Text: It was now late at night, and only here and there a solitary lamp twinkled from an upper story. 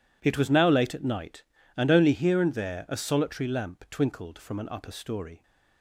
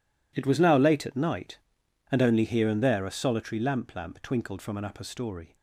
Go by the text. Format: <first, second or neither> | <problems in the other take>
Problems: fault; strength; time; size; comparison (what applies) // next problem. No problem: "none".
first | says "lamp" twice; at 3.9 s